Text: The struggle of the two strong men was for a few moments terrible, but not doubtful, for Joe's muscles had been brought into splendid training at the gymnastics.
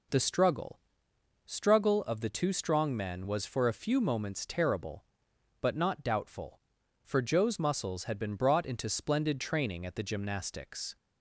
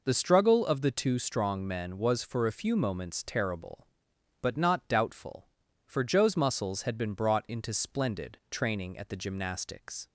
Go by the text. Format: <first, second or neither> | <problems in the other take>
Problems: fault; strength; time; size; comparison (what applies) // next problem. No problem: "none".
second | says "struggle" twice; at 1.4 s